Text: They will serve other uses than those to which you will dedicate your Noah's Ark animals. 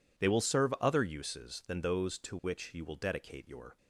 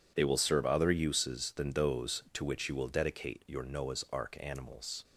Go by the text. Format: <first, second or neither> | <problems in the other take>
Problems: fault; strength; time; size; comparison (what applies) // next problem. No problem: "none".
second | stops before "Noah's Ark animals"; at 3.7 s